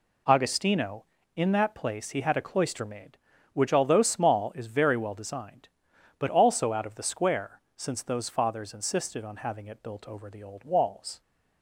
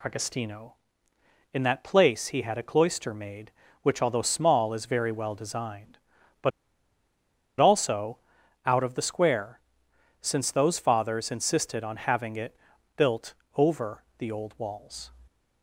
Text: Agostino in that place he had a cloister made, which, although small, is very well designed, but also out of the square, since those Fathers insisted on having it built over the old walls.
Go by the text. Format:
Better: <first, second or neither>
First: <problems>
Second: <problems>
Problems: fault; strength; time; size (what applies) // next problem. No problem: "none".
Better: first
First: none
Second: pauses between "but" and "also"; at 6.5 s; 1.1 s long // pauses between "also" and "out"; noticeable; at 8.1 s; 0.48 s long // pauses between "it" and "built"; at 12.5 s; 0.40 s long // pauses between "built" and "over"; slight; at 13.3 s; 0.22 s long